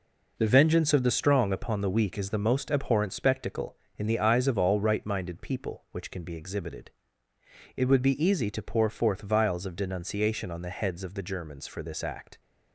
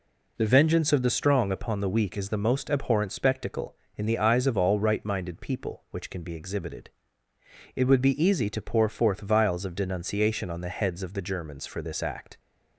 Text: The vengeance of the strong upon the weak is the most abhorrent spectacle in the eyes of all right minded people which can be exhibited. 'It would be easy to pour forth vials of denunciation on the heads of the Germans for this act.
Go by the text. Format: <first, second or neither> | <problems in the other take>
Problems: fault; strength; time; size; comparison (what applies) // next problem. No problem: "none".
second | gets quieter; strong; throughout; 7.5 dB